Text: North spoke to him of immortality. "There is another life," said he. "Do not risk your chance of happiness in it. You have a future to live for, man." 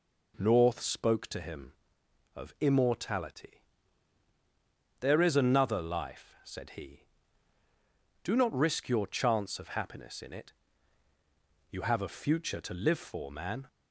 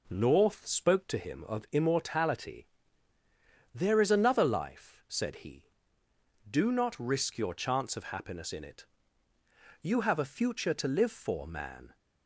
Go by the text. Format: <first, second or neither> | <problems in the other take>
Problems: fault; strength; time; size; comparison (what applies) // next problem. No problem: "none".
neither | none